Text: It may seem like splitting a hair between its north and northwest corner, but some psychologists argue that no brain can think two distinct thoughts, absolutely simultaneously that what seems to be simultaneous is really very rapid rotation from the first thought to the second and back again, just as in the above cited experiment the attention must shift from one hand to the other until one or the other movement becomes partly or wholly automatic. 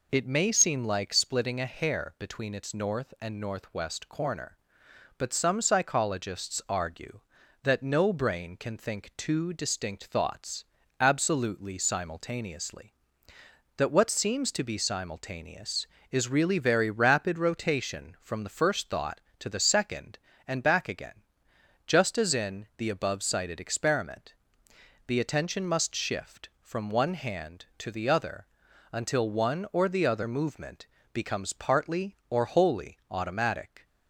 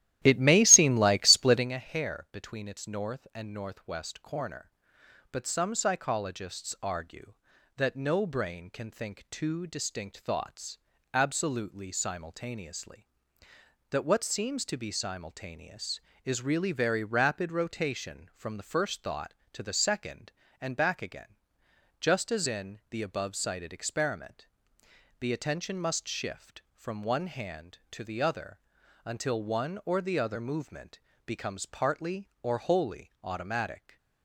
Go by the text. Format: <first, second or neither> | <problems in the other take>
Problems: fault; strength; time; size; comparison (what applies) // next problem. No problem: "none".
first | starts louder than the rest; strong; until 1.7 s; 13.5 dB // pauses between "experiment" and "the"; noticeable; at 24.4 s; 0.74 s long; noticeable in the first // pauses between "other" and "until"; at 28.5 s; 0.44 s long; also in the first // pauses between "movement" and "becomes"; slight; at 30.9 s; 0.26 s long; slight in the first